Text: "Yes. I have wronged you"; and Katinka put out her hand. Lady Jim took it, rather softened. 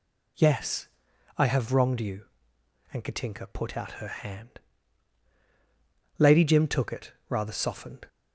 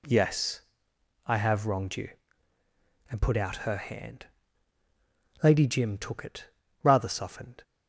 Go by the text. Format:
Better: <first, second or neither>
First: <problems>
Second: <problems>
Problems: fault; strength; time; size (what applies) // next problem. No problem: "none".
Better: first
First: none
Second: skips "Katinka"; at 3.2 s